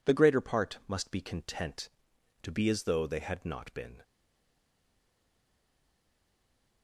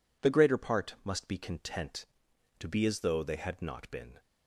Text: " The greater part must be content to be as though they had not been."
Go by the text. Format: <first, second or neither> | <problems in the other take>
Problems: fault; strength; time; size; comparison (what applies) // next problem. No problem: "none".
second | stays silent after the last word; strong; from 4.0 s on; 2.8 s long